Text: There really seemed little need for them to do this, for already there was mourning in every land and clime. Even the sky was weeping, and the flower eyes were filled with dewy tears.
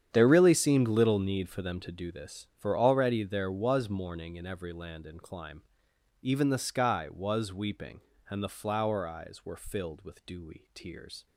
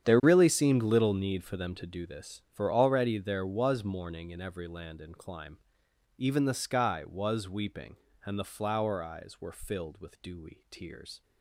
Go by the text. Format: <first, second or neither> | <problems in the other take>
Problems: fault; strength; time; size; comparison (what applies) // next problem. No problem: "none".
neither | starts louder than the rest; strong; the same in both